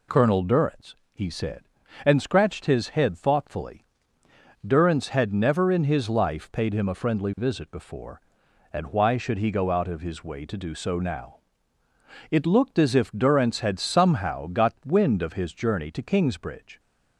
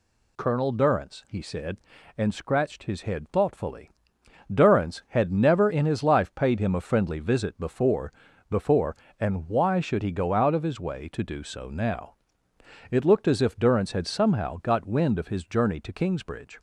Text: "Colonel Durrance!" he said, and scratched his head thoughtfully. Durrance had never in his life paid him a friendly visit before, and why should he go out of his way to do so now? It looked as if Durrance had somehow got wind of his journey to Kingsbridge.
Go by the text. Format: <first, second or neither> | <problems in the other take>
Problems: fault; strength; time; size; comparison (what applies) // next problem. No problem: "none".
first | says "before" twice; at 8.4 s